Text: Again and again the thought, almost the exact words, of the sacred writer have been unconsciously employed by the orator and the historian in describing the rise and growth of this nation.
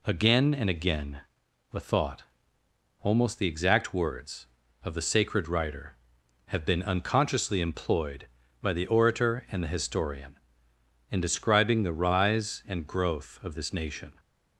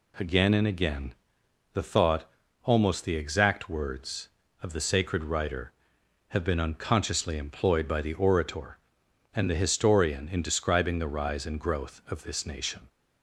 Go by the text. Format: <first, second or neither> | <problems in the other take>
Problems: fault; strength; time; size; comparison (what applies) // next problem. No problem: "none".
neither | pauses between "again" and "the"; noticeable; the same in both